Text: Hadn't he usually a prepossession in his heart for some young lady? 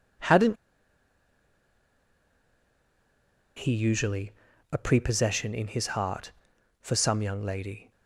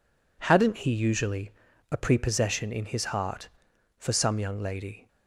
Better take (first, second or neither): second